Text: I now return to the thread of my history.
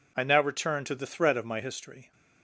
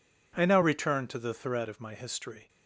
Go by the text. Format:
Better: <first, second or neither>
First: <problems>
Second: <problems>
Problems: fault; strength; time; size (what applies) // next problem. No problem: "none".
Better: neither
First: none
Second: none